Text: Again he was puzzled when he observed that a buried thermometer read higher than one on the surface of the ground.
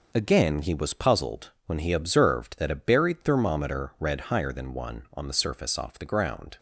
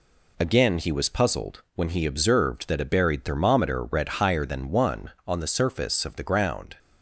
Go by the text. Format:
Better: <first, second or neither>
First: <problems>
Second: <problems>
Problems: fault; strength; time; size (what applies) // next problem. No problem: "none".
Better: second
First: pauses between "puzzled" and "when"; slight; at 1.5 s; 0.16 s long // says "off" for "of"; at 5.7 s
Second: none